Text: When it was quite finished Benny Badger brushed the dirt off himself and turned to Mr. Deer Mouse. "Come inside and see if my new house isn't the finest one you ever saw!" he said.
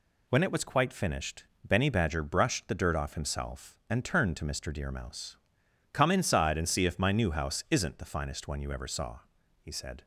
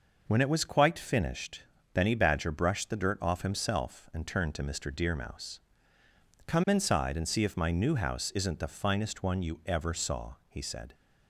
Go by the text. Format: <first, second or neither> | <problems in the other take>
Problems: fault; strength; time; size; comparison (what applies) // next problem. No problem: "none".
neither | pauses between "finished" and "Benny"; slight; the same in both